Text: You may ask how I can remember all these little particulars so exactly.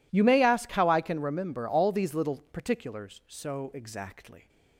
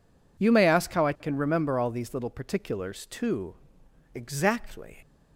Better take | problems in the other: first | says "too" for "so"; at 3.0 s

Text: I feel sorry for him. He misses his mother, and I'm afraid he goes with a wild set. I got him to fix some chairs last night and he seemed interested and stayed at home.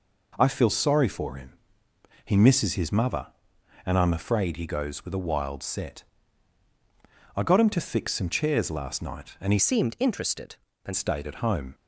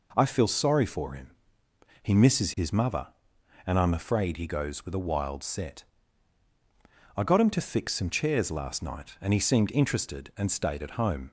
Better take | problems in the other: second | changes voice from "seemed" to "and"; from 9.5 to 10.9 s; 1.4 s long

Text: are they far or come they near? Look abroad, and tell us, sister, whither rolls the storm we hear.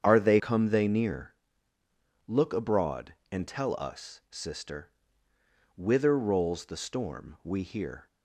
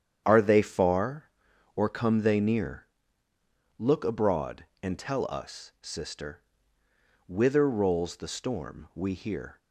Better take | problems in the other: second | starts louder than the rest; strong; until 1.0 s; 8 dB; strong in the second // skips "far or"; at 0.3 s

